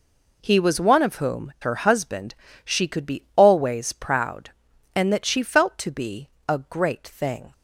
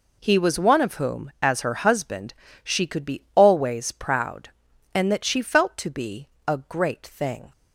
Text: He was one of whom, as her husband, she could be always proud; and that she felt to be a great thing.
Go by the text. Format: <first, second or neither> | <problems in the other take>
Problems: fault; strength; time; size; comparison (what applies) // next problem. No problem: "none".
second | skips "as"; at 1.5 s // pauses between "be" and "a"; slight; at 6.2 s; 0.20 s long; slight in the second